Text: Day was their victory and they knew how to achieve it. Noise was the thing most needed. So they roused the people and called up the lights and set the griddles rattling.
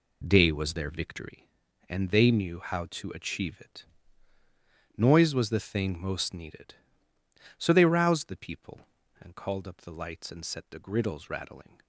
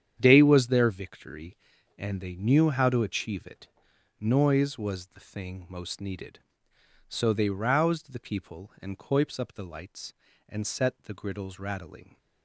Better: first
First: none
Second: starts louder than the rest; strong; until 1.1 s; 9 dB // says "coips" for "called"; at 8.9 s

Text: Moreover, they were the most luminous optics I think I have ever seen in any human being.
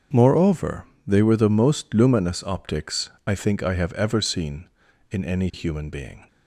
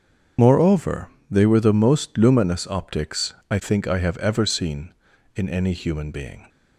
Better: first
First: starts louder than the rest; strong; until 1.3 s; 7 dB // pauses between "optics" and "I"; slight; at 3.0 s; 0.16 s long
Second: loses the start of "Moreover"; at 0.3 s; 40 ms // starts louder than the rest; strong; until 1.6 s; 7 dB // pauses between "optics" and "I"; slight; at 3.3 s; 0.16 s long

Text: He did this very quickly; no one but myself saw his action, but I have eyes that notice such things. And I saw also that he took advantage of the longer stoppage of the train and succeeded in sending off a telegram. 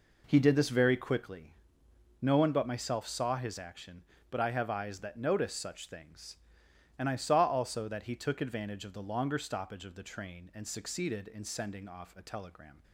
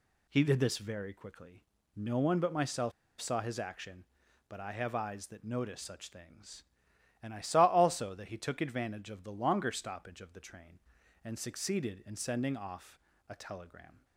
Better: first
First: none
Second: pauses between "myself" and "saw"; slight; at 2.9 s; 0.28 s long // pauses between "off" and "a"; slight; at 13.0 s; 0.28 s long

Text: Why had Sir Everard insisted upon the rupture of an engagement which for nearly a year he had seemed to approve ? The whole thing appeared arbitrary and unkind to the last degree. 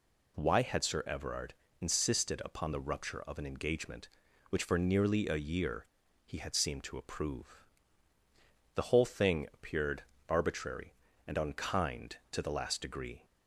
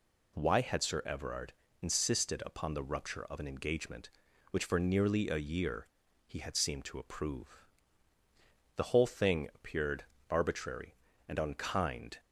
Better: first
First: pauses between "Everard" and "insisted"; slight; at 1.5 s; 0.24 s long // pauses between "year" and "he"; at 5.8 s; 0.38 s long // pauses between "appeared" and "arbitrary"; slight; at 10.0 s; 0.24 s long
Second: pauses between "Everard" and "insisted"; slight; at 1.5 s; 0.26 s long // pauses between "year" and "he"; at 5.8 s; 0.38 s long // pauses between "appeared" and "arbitrary"; slight; at 10.0 s; 0.24 s long // stops before "to the last degree"; at 12.1 s

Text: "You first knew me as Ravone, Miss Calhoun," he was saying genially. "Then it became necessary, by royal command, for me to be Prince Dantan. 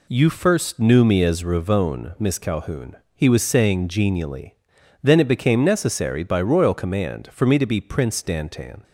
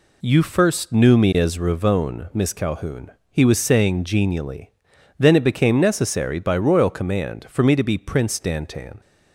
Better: neither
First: none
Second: none

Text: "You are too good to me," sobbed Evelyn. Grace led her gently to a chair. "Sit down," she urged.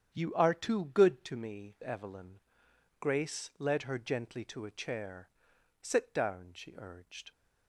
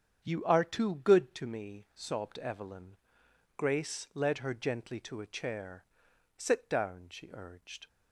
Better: second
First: starts louder than the rest; strong; until 1.1 s; 8.5 dB // skips "sobbed"; at 1.7 s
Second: starts louder than the rest; strong; until 1.2 s; 8 dB

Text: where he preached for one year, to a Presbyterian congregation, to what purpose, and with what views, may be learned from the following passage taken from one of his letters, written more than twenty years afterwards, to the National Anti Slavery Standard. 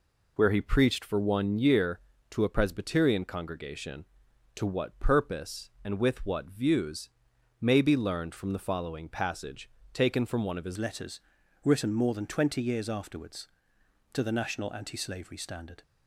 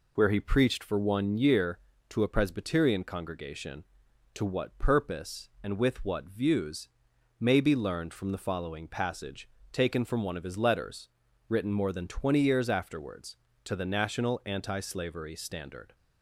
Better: second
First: pauses between "passage" and "taken"; slight; at 9.6 s; 0.24 s long // changes voice at "letters"; from 10.7 s on; 5.1 s long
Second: pauses between "passage" and "taken"; slight; at 9.4 s; 0.24 s long

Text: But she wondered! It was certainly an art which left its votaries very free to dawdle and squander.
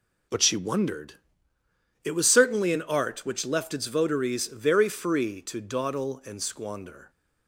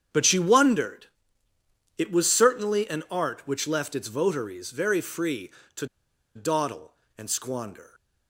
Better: first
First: none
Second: starts louder than the rest; strong; until 2.0 s; 8 dB // pauses between "to" and "dawdle"; noticeable; at 5.8 s; 0.50 s long

